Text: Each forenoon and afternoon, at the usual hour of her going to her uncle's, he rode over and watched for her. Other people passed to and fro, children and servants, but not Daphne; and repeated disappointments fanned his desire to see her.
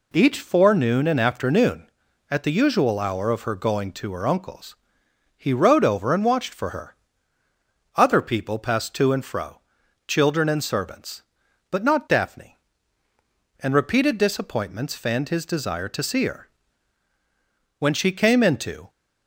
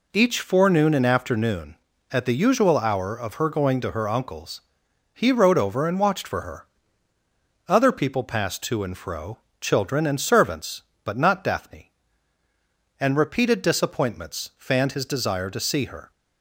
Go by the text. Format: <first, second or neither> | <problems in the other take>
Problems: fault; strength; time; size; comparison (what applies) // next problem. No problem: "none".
second | goes on to say "When she came into"; noticeable; from 17.7 s on; 1.1 s long